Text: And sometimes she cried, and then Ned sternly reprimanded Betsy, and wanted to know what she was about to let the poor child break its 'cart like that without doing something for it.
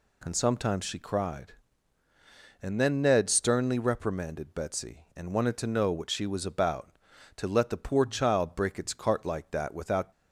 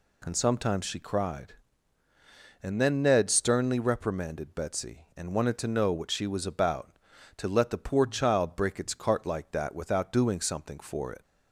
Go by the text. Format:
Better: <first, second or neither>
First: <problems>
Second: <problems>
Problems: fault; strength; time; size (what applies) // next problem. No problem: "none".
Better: second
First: stops before "doing something for it"; at 10.1 s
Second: none